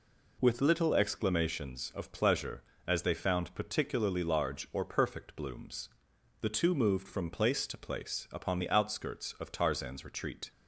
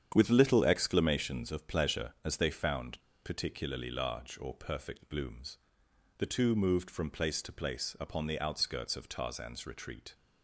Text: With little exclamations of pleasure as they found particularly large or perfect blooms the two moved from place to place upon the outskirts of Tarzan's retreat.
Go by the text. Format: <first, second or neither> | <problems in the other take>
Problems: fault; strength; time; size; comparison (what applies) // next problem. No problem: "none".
first | starts louder than the rest; strong; until 1.1 s; 8.5 dB // pauses between "found" and "particularly"; slight; at 3.0 s; 0.23 s long // pauses between "blooms" and "the"; noticeable; at 5.5 s; 0.60 s long; noticeable in the first